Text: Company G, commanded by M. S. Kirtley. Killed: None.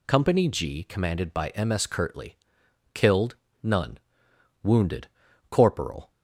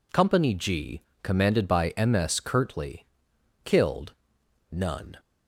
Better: second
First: goes on to say "Wounded Corporal"; from 4.6 s on; 1.4 s long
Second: none

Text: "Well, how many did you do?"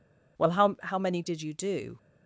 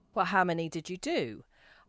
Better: second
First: says "how" twice; at 0.8 s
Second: none

